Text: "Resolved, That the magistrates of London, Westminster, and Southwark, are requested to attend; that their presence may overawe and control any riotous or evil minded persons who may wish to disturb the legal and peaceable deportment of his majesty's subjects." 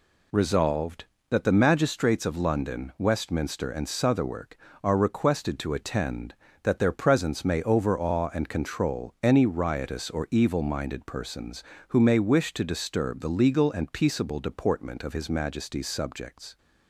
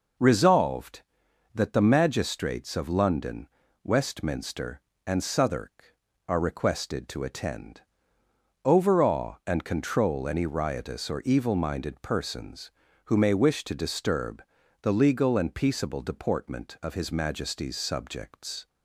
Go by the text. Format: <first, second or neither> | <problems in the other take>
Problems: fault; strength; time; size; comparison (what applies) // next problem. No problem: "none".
first | skips "that their presence may"; at 8.2 s // pauses between "disturb" and "the"; at 14.4 s; 0.38 s long